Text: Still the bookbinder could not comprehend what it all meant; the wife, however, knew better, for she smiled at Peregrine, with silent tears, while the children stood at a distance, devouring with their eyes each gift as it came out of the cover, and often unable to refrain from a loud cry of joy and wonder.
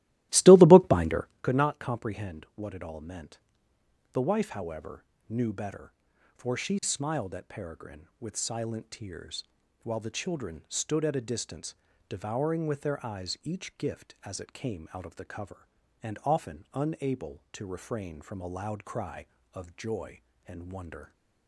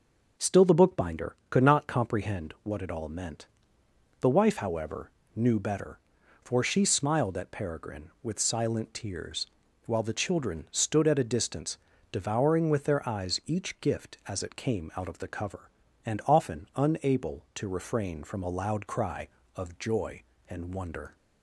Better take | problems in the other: second | starts louder than the rest; strong; until 1.5 s; 16.5 dB

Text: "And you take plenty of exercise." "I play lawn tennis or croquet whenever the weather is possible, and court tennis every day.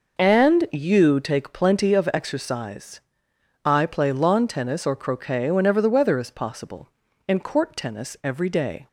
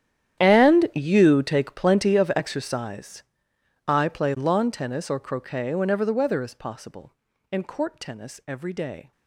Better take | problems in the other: first | gets quieter; strong; throughout; 19 dB

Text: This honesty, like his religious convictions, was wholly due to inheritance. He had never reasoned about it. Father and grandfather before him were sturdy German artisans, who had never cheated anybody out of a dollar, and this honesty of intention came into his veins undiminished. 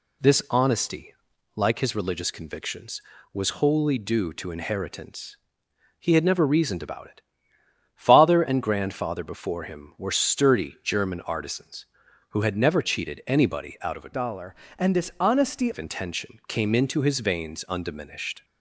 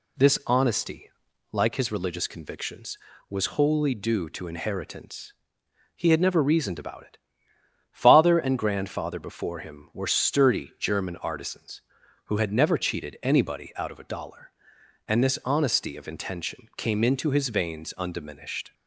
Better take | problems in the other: second | changes voice from "dollar" to "honesty"; from 14.1 to 15.7 s; 1.6 s long

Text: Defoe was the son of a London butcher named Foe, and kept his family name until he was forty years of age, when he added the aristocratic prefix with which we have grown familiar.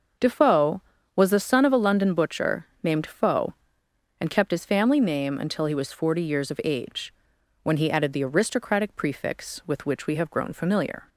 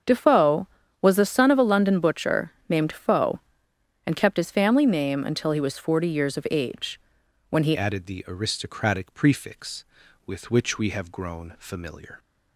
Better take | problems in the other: first | starts louder than the rest; until 1.3 s; 7 dB; noticeable in the first // pauses between "butcher" and "named"; slight; at 2.5 s; 0.16 s long; slight in the first // changes voice at "added"; from 7.7 s on; 4.4 s long

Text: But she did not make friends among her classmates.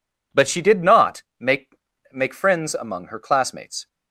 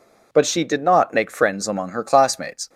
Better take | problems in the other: second | pauses between "not" and "make"; slight; at 1.2 s; 0.16 s long // says "make" twice; at 2.1 s

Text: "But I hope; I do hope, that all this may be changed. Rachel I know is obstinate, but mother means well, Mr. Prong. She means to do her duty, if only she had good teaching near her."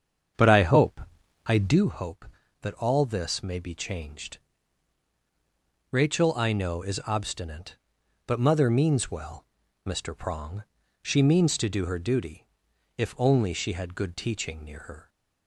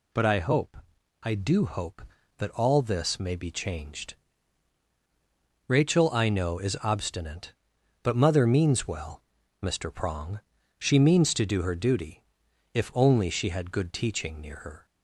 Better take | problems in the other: second | starts louder than the rest; strong; until 1.9 s; 7.5 dB

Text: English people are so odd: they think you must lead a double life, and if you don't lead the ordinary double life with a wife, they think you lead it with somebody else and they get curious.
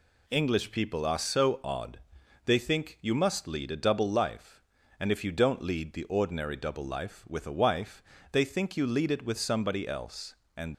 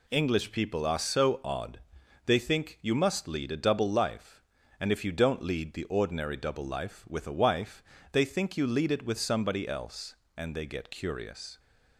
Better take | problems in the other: second | stops before "they get curious"; at 10.7 s

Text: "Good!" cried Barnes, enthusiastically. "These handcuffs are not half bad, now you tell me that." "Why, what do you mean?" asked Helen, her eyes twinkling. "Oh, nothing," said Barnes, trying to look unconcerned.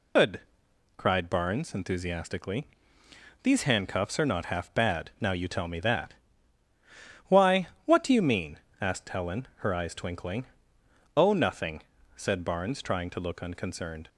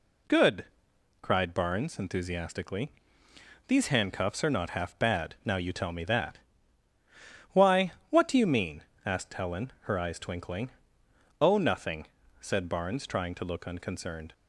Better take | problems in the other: second | loses the start of "Good"; at 0.1 s; 135 ms

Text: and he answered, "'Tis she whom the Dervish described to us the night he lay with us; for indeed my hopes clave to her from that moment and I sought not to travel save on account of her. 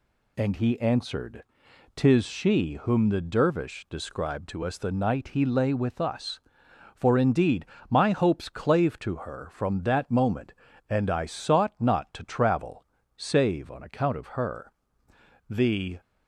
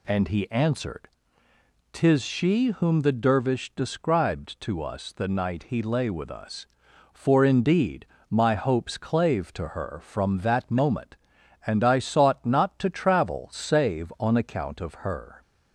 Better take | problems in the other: second | pauses between "indeed" and "my"; slight; at 7.6 s; 0.24 s long; slight in the second // pauses between "travel" and "save"; slight; at 12.8 s; 0.32 s long // goes on to say "The"; from 15.4 s on; 0.52 s long

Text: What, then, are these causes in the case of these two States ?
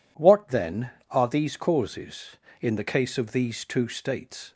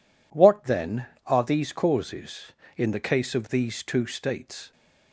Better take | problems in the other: neither | none

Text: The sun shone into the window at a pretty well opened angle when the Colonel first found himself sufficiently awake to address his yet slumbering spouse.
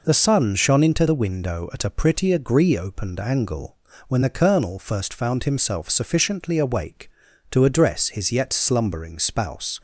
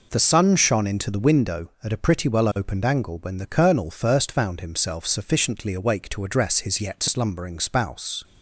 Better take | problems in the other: second | says "agree" for "well"; at 2.3 s // pauses between "angle" and "when"; slight; at 3.7 s; 0.32 s long

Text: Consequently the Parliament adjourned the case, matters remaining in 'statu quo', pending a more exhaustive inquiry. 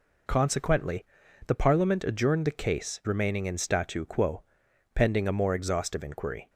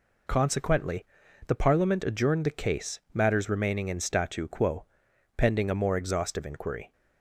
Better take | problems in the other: second | pauses between "Consequently" and "the"; at 1.0 s; 0.44 s long; also in the second // skips "matters"; at 3.0 s

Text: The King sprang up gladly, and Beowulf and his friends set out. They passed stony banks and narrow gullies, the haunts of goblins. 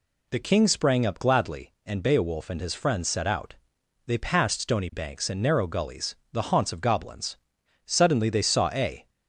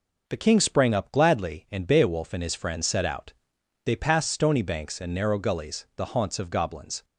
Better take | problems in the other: second | goes on to say "Suddenly they saw a"; noticeable; from 7.8 s on; 1.2 s long

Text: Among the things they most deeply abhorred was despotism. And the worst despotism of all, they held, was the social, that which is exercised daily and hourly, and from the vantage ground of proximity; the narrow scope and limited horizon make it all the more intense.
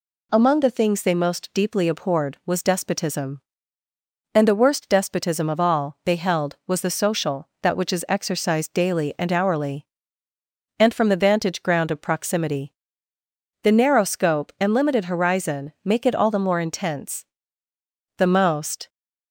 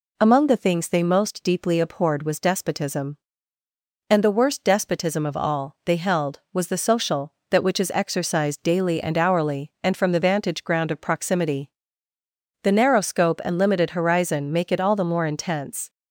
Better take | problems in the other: second | goes on to say "The most"; noticeable; from 18.1 s on; 0.72 s long

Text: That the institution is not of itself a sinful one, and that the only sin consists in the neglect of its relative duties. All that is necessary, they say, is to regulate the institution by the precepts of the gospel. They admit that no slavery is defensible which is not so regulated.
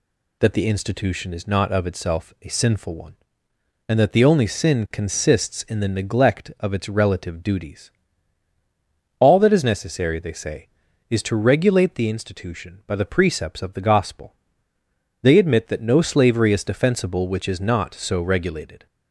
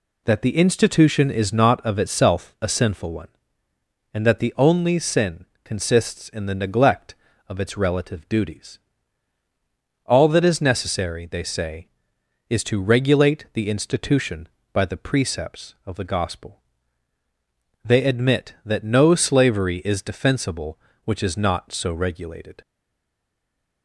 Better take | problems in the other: first | pauses between "sin" and "consists"; slight; at 5.4 s; 0.21 s long // stays silent after the last word; noticeable; from 22.6 s on; 1.2 s long

